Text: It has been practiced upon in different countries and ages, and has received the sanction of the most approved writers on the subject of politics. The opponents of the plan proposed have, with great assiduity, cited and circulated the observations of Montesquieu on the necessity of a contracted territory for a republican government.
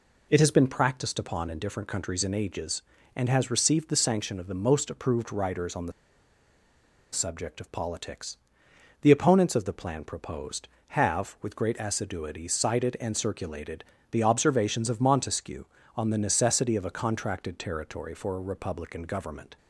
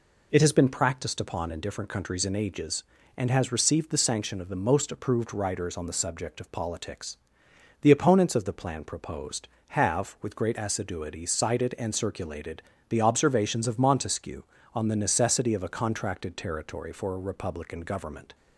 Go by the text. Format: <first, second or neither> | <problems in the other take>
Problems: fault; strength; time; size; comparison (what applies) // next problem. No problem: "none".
second | pauses between "the" and "subject"; at 5.9 s; 1.2 s long // pauses between "circulated" and "the"; slight; at 13.8 s; 0.28 s long; slight in the second